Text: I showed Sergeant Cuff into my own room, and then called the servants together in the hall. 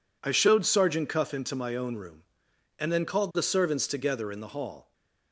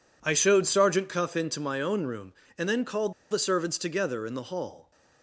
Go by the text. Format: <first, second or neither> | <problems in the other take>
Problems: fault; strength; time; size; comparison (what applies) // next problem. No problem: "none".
first | pauses between "called" and "the"; slight; at 3.1 s; 0.17 s long